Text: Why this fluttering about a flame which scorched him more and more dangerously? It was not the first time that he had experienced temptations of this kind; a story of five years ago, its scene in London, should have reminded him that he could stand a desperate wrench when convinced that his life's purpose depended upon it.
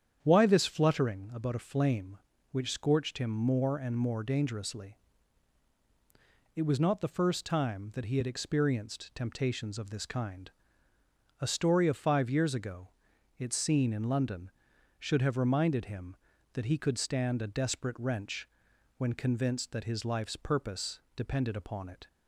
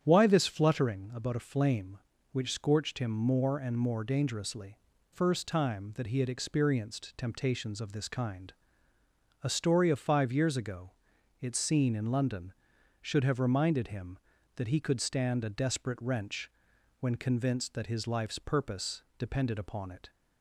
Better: first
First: starts louder than the rest; strong; until 1.2 s; 8.5 dB // pauses between "wrench" and "when"; noticeable; at 18.4 s; 0.52 s long // pauses between "purpose" and "depended"; slight; at 20.9 s; 0.16 s long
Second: starts louder than the rest; strong; until 1.0 s; 9 dB // skips "It was not the"; at 4.9 s // pauses between "wrench" and "when"; noticeable; at 16.4 s; 0.52 s long // pauses between "purpose" and "depended"; slight; at 19.0 s; 0.16 s long

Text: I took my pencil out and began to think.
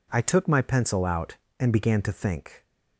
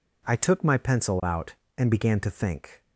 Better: neither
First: none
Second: none

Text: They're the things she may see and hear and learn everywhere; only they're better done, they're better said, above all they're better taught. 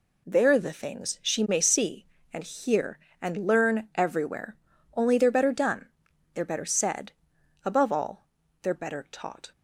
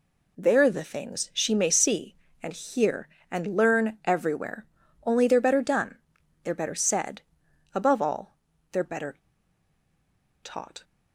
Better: first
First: pauses between "all" and "they're"; slight; at 8.2 s; 0.34 s long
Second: pauses between "all" and "they're"; slight; at 8.3 s; 0.34 s long // pauses between "better" and "taught"; strong; at 9.1 s; 1.2 s long

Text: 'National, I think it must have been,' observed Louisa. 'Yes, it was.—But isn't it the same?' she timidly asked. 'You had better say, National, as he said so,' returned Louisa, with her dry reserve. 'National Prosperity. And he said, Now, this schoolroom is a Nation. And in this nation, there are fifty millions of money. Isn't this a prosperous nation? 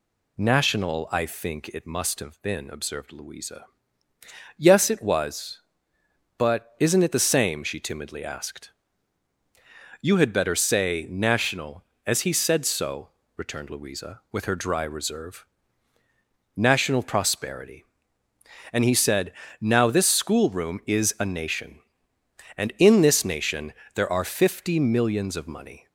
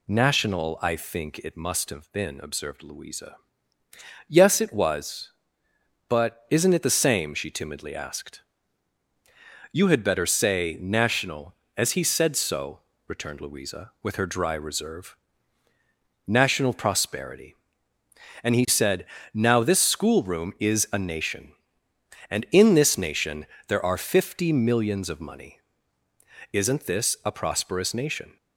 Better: second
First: stops before "Isn't this a prosperous nation"; at 25.8 s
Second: none

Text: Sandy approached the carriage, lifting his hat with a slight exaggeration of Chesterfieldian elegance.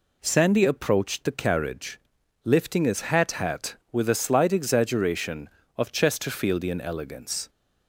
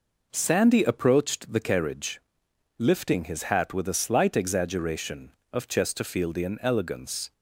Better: second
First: says "hat" twice; at 3.3 s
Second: none

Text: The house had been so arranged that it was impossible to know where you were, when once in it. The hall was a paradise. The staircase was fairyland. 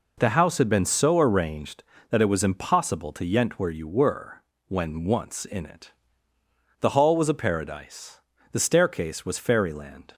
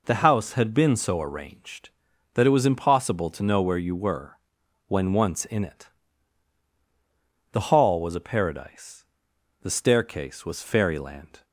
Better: second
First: says "yent" for "know"; at 3.2 s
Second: none

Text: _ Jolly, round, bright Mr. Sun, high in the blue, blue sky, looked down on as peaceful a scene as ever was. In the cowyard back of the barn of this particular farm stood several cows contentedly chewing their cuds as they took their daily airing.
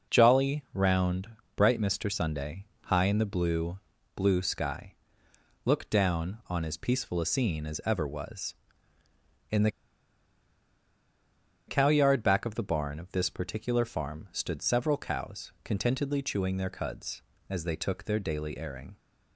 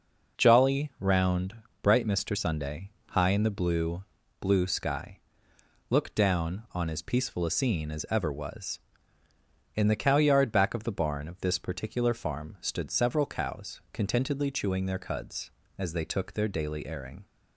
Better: second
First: pauses between "the" and "cowyard"; strong; at 9.6 s; 1.9 s long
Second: none

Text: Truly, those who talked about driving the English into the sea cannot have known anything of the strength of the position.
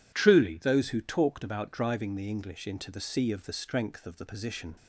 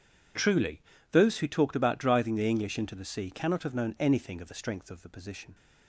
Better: second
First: skips "cannot have known anything"; at 3.3 s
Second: none

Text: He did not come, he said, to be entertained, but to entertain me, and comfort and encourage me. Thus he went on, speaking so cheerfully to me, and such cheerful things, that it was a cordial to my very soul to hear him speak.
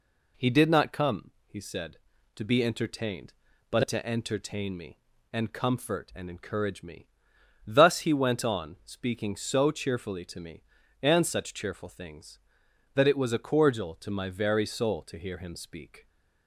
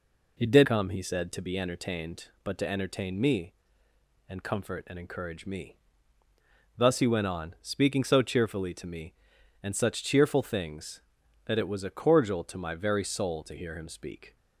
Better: first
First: none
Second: skips "not"; at 0.6 s

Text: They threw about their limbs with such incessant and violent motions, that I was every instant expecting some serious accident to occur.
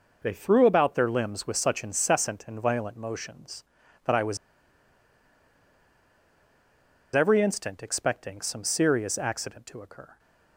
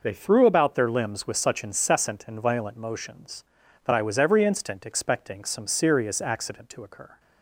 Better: second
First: pauses between "was" and "every"; strong; at 4.3 s; 2.7 s long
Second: none

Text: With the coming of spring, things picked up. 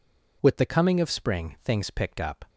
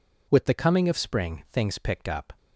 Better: neither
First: none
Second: none

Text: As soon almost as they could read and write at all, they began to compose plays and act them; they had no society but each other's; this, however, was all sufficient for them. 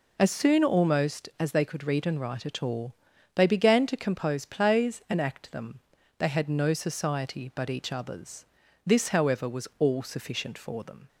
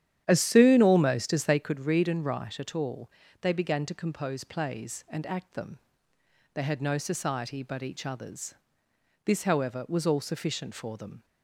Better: first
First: none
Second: starts louder than the rest; strong; until 1.8 s; 10.5 dB

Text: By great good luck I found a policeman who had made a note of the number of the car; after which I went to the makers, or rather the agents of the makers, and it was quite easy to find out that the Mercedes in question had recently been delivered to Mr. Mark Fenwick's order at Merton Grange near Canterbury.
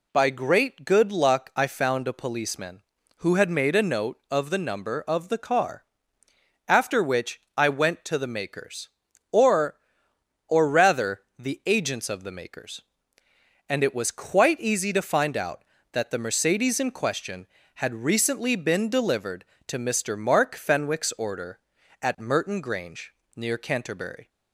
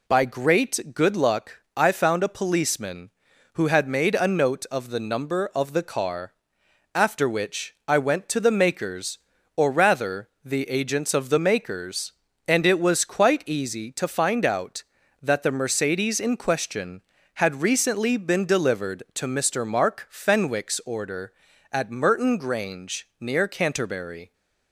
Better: second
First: pauses between "which" and "I"; slight; at 7.3 s; 0.16 s long // says "or" twice; at 10.4 s // pauses between "rather" and "the"; slight; at 11.2 s; 0.16 s long // pauses between "Grange" and "near"; slight; at 23.1 s; 0.20 s long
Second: pauses between "rather" and "the"; slight; at 10.2 s; 0.16 s long

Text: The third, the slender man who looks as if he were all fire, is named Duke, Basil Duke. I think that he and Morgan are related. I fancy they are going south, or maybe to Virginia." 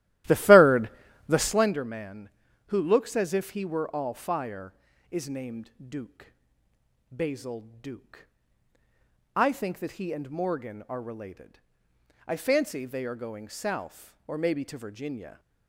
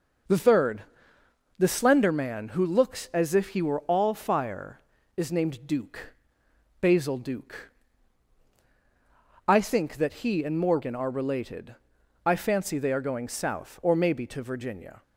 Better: second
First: starts louder than the rest; strong; until 1.6 s; 15 dB // pauses between "named" and "Duke"; slight; at 5.6 s; 0.18 s long // pauses between "Basil" and "Duke"; slight; at 7.6 s; 0.18 s long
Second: none

